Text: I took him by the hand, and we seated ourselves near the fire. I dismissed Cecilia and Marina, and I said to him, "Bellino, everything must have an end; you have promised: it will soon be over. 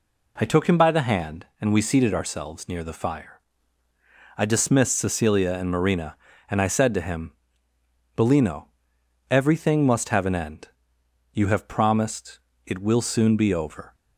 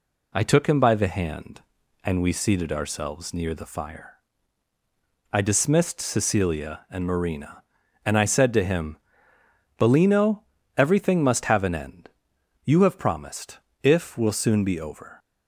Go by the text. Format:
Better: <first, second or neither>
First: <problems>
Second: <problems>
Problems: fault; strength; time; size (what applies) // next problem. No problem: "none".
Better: first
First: none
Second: says "if" for "it"; at 13.8 s